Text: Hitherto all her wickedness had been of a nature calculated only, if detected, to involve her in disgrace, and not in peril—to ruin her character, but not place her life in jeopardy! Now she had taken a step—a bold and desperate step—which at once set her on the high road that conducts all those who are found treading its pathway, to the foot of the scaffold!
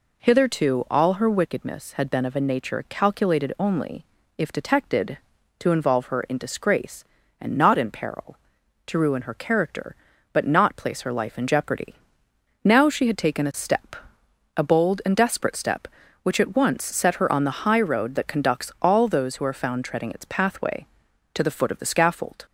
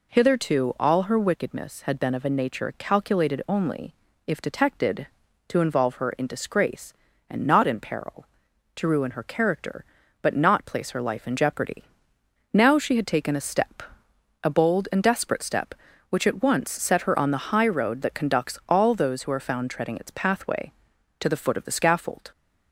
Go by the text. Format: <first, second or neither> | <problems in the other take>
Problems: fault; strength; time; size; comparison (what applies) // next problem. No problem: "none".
neither | none